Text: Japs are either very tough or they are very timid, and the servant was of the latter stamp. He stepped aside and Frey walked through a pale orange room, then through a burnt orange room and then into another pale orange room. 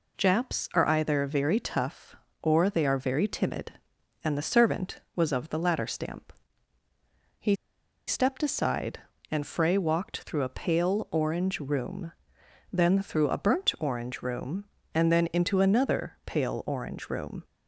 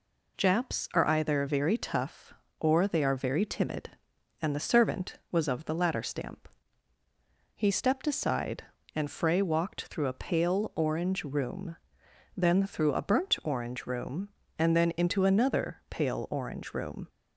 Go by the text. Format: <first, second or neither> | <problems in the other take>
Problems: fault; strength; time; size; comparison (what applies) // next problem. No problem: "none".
second | pauses between "He" and "stepped"; noticeable; at 7.5 s; 0.53 s long